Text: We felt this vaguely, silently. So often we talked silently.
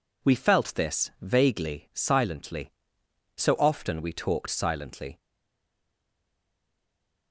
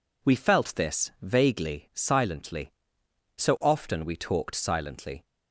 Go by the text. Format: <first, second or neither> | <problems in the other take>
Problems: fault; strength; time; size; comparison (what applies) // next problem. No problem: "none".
second | stays silent after the last word; from 5.1 s on; 2.2 s long